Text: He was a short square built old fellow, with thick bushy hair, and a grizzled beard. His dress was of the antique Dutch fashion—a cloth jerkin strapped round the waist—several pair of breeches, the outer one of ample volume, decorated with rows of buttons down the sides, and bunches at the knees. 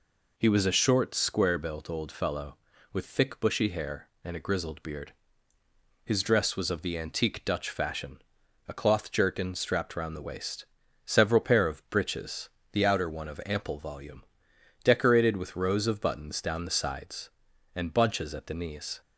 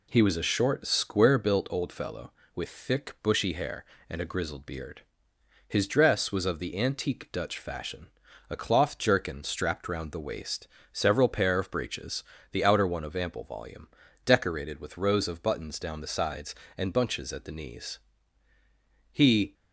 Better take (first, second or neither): first